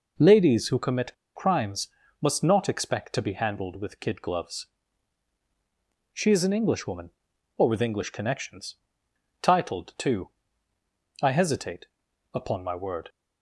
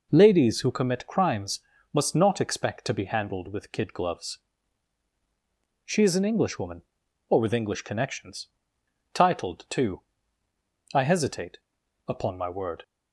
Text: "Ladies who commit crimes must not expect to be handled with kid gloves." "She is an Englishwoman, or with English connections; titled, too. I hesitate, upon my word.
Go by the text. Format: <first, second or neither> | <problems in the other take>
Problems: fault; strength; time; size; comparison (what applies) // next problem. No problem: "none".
second | pauses between "commit" and "crimes"; slight; at 1.1 s; 0.23 s long // pauses between "crimes" and "must"; slight; at 1.8 s; 0.34 s long; slight in the second